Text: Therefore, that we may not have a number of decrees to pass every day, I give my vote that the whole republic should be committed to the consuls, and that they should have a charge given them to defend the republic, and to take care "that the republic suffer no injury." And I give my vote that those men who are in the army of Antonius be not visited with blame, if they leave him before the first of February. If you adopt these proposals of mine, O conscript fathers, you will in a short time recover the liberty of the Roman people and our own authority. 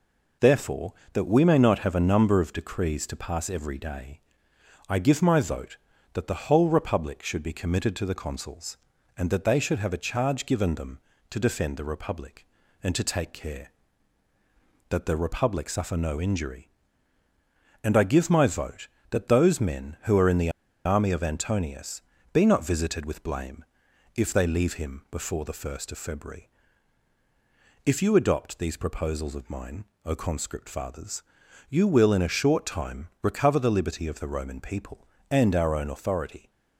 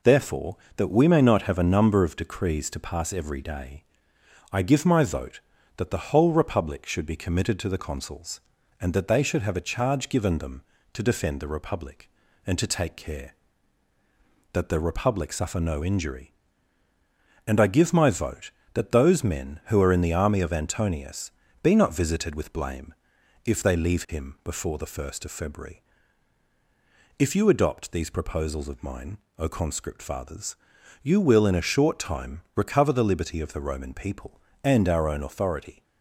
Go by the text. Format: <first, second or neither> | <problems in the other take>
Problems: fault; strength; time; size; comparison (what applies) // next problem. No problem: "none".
second | pauses between "the" and "army"; slight; at 20.4 s; 0.35 s long // pauses between "Antonius" and "be"; slight; at 22.0 s; 0.32 s long; slight in the second